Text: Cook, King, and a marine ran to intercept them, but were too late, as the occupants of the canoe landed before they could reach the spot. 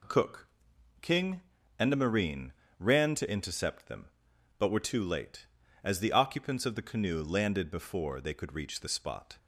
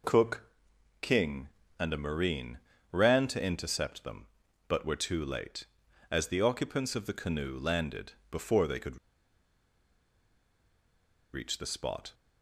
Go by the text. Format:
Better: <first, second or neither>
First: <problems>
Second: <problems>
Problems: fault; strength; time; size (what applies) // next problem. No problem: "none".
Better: first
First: pauses between "marine" and "ran"; slight; at 2.5 s; 0.28 s long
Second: pauses between "marine" and "ran"; slight; at 2.5 s; 0.32 s long // pauses between "landed" and "before"; slight; at 8.1 s; 0.16 s long // pauses between "could" and "reach"; strong; at 8.9 s; 2.3 s long